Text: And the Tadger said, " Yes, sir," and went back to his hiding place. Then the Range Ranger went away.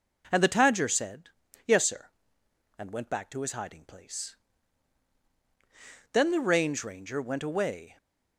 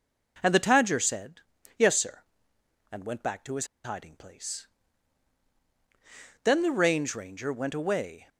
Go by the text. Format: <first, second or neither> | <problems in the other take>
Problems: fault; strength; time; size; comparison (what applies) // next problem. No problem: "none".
first | pauses between "his" and "hiding"; slight; at 3.6 s; 0.19 s long